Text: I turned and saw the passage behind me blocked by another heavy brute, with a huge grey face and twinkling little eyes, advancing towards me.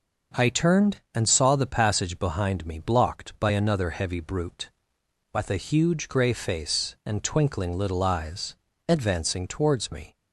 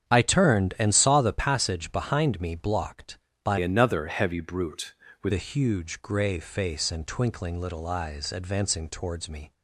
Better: first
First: none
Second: starts louder than the rest; strong; until 1.1 s; 8.5 dB // changes voice from "another" to "with"; from 3.5 to 5.3 s; 1.8 s long

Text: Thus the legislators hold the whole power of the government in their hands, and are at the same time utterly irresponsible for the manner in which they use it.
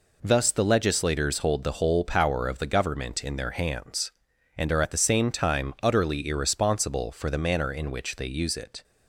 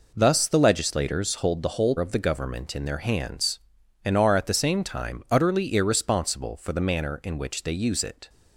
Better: first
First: none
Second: skips "power"; at 1.9 s

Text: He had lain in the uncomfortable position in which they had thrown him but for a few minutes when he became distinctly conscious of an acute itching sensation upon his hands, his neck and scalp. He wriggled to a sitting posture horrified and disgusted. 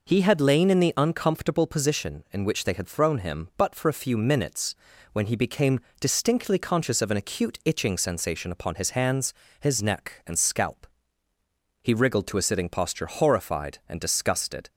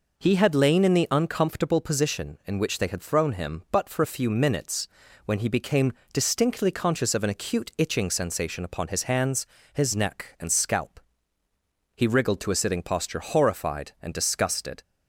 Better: neither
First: pauses between "minutes" and "when"; at 4.7 s; 0.38 s long // pauses between "became" and "distinctly"; slight; at 5.7 s; 0.20 s long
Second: pauses between "minutes" and "when"; at 4.8 s; 0.38 s long // pauses between "became" and "distinctly"; slight; at 5.9 s; 0.20 s long

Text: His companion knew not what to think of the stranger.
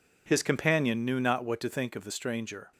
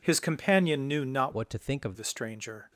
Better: first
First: none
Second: changes voice from "what" to "of"; from 1.3 to 1.9 s; 0.6 s long

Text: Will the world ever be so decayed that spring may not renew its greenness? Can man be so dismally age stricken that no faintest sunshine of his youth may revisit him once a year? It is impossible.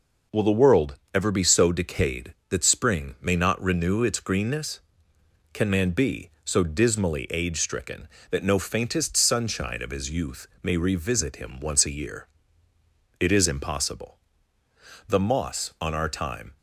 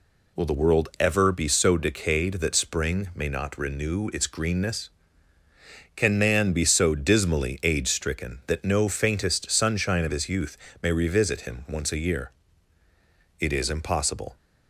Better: second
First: pauses between "world" and "ever"; slight; at 0.9 s; 0.16 s long // pauses between "youth" and "may"; slight; at 10.4 s; 0.16 s long // goes on to say "The moss on our time"; from 15.0 s on; 1.5 s long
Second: pauses between "youth" and "may"; slight; at 10.5 s; 0.26 s long

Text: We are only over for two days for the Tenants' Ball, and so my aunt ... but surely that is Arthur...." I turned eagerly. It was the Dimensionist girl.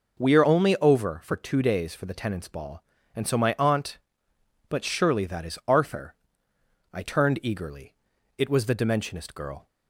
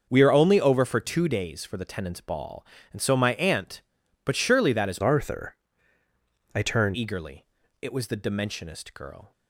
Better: first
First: none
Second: starts louder than the rest; until 1.1 s; 6.5 dB // changes voice from "Arthur" to "turned"; from 5.0 to 6.9 s; 1.9 s long

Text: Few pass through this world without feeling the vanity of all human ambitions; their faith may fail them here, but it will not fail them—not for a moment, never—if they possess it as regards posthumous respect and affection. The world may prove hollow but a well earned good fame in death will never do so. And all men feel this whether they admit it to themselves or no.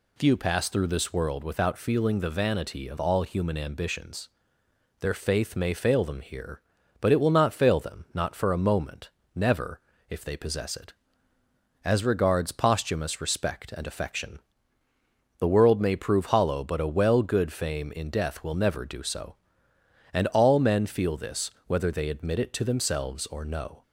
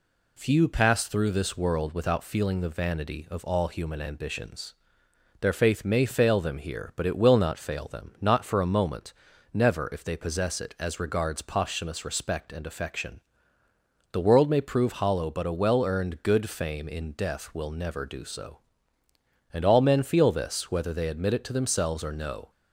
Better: second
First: skips "earned"; at 17.2 s // pauses between "this" and "whether"; slight; at 21.4 s; 0.16 s long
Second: none

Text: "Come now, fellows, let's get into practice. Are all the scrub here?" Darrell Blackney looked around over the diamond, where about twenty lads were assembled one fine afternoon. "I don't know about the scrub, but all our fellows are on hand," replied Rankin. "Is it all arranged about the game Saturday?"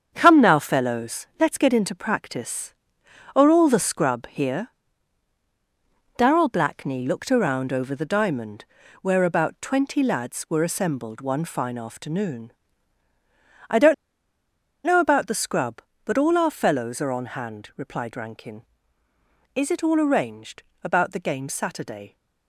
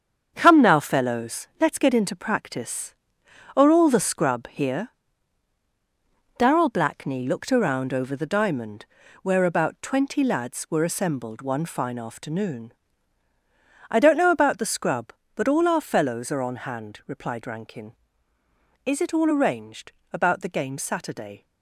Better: second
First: starts louder than the rest; strong; until 1.1 s; 7.5 dB // pauses between "don't" and "know"; noticeable; at 13.9 s; 0.90 s long // pauses between "arranged" and "about"; slight; at 20.6 s; 0.20 s long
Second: starts louder than the rest; strong; until 1.3 s; 7.5 dB // pauses between "arranged" and "about"; slight; at 19.9 s; 0.20 s long

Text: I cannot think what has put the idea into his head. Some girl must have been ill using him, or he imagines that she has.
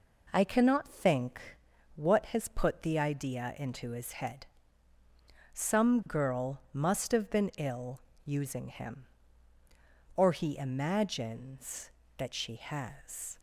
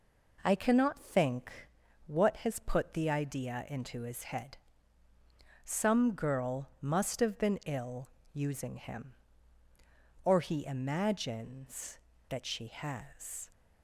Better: neither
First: pauses between "think" and "what"; noticeable; at 1.4 s; 0.56 s long // pauses between "ill" and "using"; slight; at 7.9 s; 0.26 s long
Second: pauses between "think" and "what"; noticeable; at 1.5 s; 0.56 s long // pauses between "ill" and "using"; slight; at 8.0 s; 0.26 s long

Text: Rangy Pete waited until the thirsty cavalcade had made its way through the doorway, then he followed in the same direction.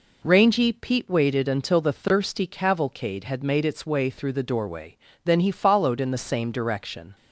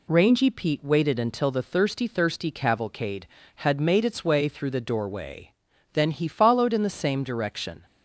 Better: first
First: none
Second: says "thirsty" twice; at 2.0 s

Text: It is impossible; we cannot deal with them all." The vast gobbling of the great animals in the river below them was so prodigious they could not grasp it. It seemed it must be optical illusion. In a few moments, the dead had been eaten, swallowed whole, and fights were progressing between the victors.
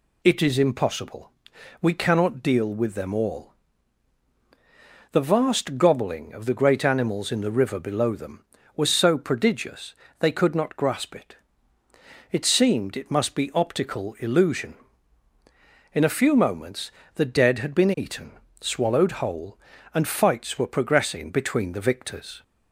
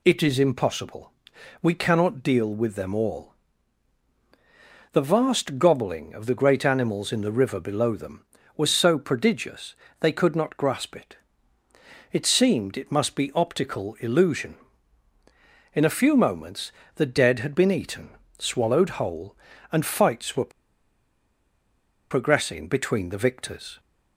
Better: first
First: pauses between "prodigious" and "they"; slight; at 9.9 s; 0.24 s long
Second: pauses between "prodigious" and "they"; slight; at 9.7 s; 0.24 s long // pauses between "were" and "progressing"; strong; at 20.5 s; 1.6 s long

